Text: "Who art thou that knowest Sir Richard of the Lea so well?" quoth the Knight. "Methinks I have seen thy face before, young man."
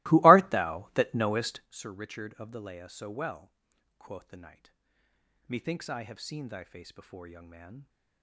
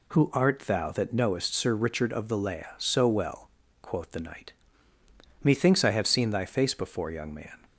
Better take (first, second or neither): second